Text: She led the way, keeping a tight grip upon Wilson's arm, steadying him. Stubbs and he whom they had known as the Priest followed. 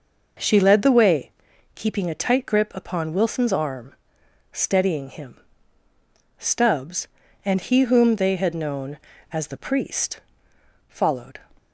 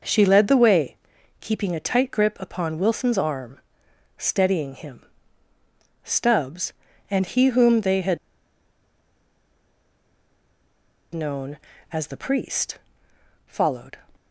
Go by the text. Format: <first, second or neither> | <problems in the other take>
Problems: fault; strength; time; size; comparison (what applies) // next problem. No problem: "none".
first | pauses between "had" and "known"; strong; at 8.1 s; 2.9 s long // pauses between "Priest" and "followed"; noticeable; at 12.7 s; 0.68 s long; noticeable in the first